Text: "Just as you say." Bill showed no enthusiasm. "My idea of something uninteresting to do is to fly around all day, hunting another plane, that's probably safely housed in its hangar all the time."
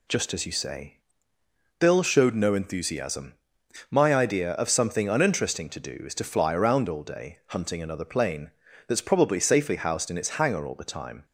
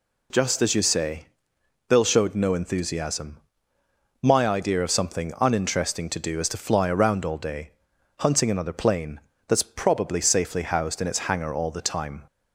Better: neither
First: none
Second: none

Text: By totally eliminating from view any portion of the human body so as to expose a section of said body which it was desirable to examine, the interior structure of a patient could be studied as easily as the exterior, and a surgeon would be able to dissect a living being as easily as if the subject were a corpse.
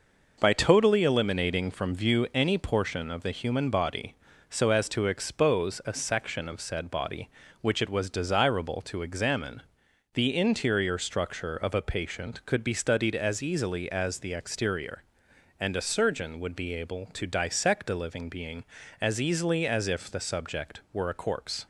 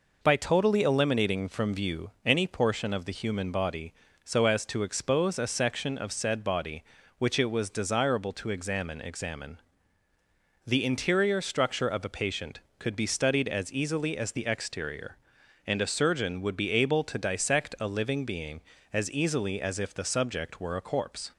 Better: first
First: none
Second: pauses between "view" and "any"; slight; at 2.1 s; 0.16 s long // says "examine" twice; at 9.0 s

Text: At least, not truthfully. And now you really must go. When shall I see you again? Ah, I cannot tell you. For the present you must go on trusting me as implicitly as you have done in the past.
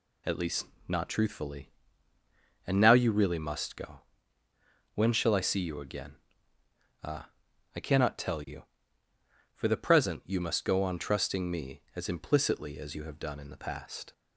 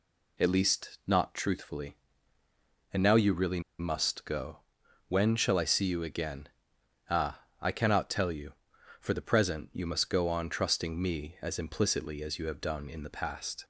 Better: first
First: none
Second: pauses between "really" and "must"; slight; at 3.6 s; 0.18 s long

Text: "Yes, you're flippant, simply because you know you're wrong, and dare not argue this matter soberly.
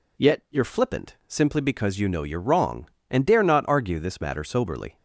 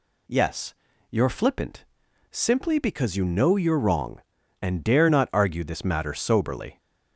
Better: second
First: says "Yet" for "Yes"; at 0.1 s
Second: none

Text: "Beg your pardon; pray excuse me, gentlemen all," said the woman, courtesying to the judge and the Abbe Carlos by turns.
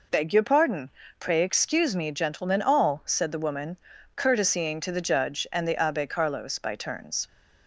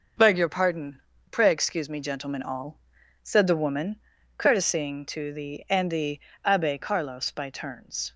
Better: first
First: none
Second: skips "judge"; at 5.6 s // pauses between "the" and "Abbe"; slight; at 6.1 s; 0.26 s long

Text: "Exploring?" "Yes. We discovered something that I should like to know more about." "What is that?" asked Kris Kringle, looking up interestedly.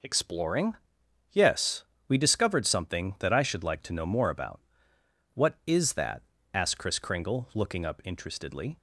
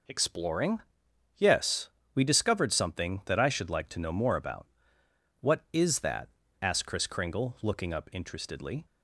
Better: neither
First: none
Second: none

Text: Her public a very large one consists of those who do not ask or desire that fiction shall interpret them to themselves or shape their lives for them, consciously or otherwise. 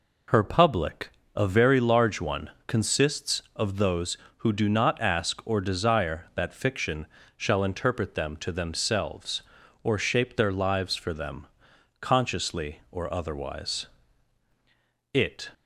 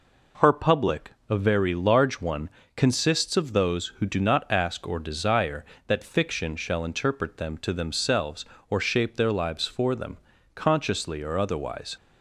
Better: second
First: pauses between "public" and "a"; slight; at 1.0 s; 0.26 s long // pauses between "one" and "consists"; slight; at 2.5 s; 0.16 s long // pauses between "fiction" and "shall"; slight; at 7.0 s; 0.28 s long // goes on to say "It"; slight; from 15.1 s on; 0.34 s long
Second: pauses between "public" and "a"; slight; at 1.1 s; 0.18 s long // pauses between "one" and "consists"; slight; at 2.5 s; 0.26 s long

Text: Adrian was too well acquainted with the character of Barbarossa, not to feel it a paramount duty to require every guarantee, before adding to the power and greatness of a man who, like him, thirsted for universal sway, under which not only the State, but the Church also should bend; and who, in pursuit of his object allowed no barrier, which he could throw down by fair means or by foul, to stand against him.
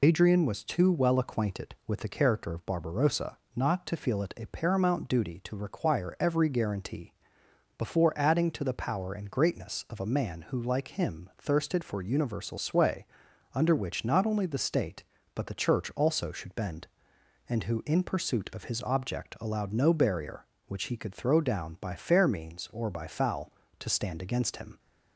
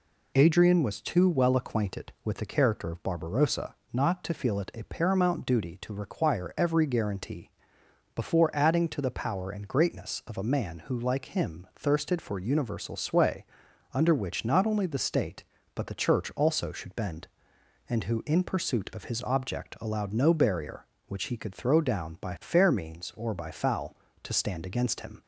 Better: second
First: loses the start of "Adrian"; at 0.0 s; 55 ms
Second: none

